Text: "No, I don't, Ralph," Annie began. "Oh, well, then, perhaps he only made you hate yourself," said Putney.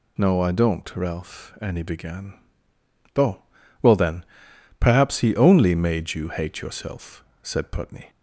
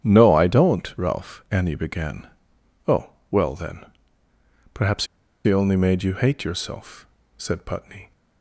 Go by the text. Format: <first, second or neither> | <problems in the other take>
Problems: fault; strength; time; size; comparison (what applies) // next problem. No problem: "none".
first | starts louder than the rest; strong; until 1.0 s; 9 dB // pauses between "perhaps" and "he"; at 5.0 s; 0.41 s long